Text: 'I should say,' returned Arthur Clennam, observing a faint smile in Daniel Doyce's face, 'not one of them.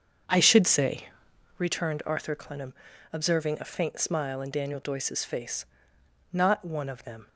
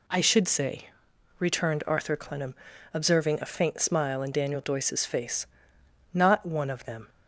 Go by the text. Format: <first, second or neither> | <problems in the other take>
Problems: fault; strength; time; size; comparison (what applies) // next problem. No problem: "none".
second | starts louder than the rest; until 1.7 s; 7 dB